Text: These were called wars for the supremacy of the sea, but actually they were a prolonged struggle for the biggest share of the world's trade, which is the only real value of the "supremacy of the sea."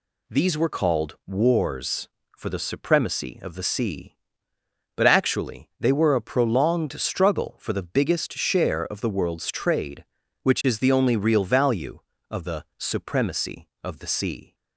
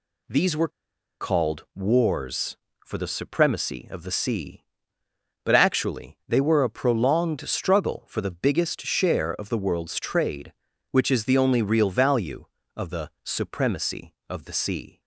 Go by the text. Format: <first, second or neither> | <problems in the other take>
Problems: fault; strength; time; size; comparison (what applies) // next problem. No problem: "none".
first | pauses between "were" and "called"; noticeable; at 0.6 s; 0.51 s long